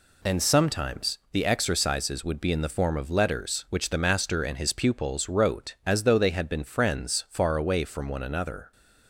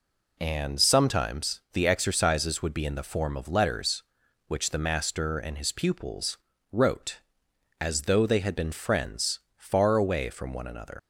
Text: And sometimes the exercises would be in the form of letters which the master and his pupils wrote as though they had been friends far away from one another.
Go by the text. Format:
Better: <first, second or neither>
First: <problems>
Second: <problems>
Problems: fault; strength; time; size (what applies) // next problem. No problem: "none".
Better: first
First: none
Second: pauses between "pupils" and "wrote"; slight; at 6.3 s; 0.34 s long // pauses between "friends" and "far"; slight; at 9.3 s; 0.18 s long // leaves "another" unfinished; at 10.9 s; 100 ms